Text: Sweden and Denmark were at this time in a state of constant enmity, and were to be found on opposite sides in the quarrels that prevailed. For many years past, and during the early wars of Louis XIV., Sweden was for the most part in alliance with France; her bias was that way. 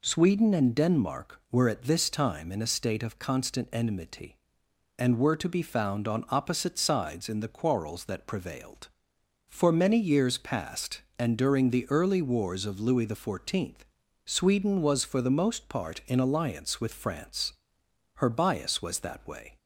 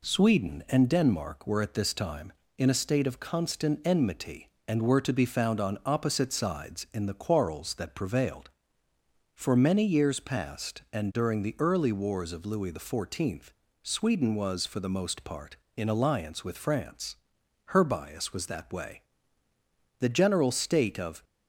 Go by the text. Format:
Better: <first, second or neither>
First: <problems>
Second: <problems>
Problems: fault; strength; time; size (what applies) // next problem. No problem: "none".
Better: first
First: none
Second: goes on to say "The general state of"; noticeable; from 19.9 s on; 1.2 s long